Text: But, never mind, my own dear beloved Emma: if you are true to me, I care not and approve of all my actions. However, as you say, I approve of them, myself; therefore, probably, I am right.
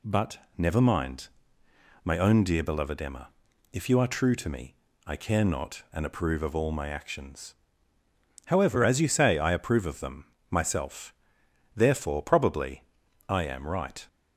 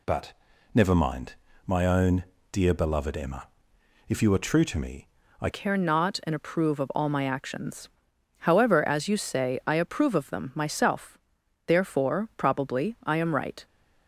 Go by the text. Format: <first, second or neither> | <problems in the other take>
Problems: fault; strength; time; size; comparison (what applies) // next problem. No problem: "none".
first | pauses between "own" and "dear"; slight; at 2.2 s; 0.28 s long // changes voice at "care"; from 5.5 s on; 8.1 s long